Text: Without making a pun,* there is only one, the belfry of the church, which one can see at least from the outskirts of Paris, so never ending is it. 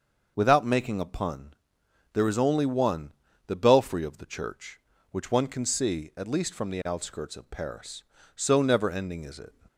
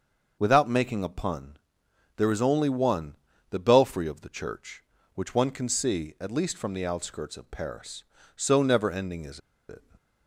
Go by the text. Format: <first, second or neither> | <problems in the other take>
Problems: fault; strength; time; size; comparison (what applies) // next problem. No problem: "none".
first | starts louder than the rest; until 1.4 s; 6 dB; also in the first // pauses between "is" and "it"; slight; at 9.3 s; 0.29 s long